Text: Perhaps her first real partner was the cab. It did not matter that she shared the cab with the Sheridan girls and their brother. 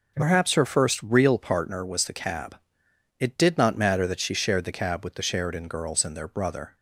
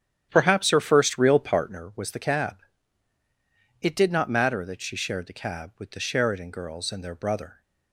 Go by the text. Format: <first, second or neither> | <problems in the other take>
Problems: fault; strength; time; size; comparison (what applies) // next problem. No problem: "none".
first | starts louder than the rest; strong; until 1.8 s; 10.5 dB